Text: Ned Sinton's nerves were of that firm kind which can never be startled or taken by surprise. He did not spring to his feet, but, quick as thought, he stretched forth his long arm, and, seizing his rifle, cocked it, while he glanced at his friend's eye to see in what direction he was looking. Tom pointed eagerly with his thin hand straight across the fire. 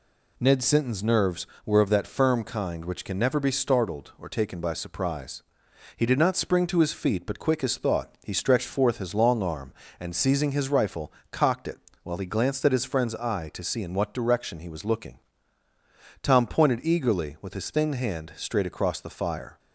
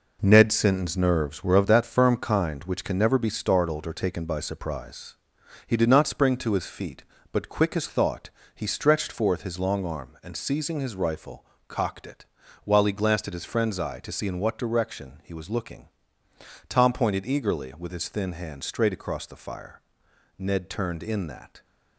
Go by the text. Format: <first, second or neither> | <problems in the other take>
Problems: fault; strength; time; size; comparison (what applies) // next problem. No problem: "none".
first | goes on to say "Ned turned in that"; noticeable; from 20.3 s on; 1.2 s long